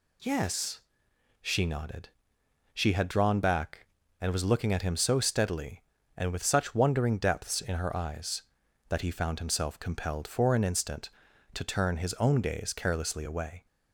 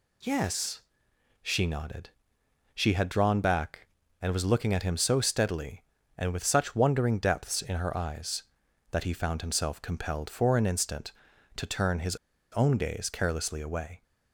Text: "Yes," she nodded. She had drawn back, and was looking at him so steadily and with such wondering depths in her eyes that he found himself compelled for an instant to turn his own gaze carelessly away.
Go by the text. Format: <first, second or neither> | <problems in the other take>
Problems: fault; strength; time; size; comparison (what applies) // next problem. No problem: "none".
first | pauses between "his" and "own"; slight; at 12.1 s; 0.35 s long